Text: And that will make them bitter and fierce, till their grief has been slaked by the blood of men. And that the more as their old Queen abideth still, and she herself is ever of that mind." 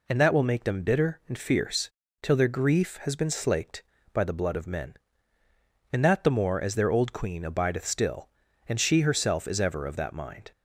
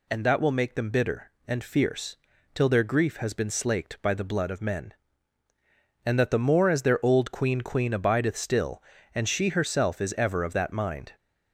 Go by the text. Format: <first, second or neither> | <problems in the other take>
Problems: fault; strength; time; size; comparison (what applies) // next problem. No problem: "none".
first | says "Queen" twice; at 7.6 s